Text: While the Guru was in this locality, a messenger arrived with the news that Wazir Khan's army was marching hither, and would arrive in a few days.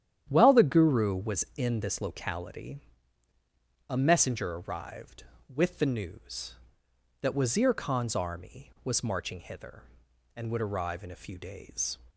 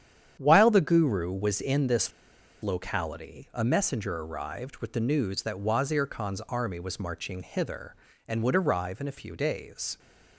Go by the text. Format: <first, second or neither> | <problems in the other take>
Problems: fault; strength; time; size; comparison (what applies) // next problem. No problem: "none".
first | starts louder than the rest; strong; until 1.4 s; 9 dB; strong in the first // pauses between "this" and "locality"; noticeable; at 2.1 s; 0.51 s long